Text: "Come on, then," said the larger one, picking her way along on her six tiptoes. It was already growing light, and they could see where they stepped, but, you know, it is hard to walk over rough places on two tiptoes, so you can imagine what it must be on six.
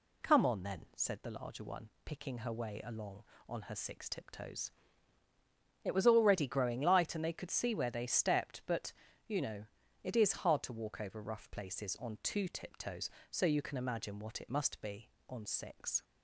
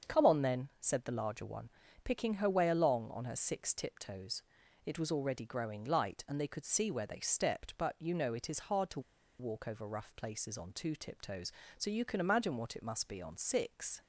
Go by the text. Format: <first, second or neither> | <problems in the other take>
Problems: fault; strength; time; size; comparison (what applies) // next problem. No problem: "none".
first | starts louder than the rest; until 1.2 s; 7 dB // pauses between "to" and "walk"; at 8.9 s; 0.39 s long